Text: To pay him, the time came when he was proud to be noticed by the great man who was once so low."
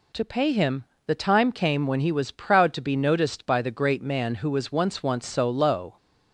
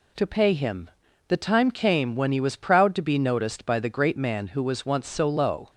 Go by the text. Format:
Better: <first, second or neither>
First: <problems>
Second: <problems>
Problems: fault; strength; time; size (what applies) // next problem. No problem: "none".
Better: second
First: says "once" twice; at 5.0 s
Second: none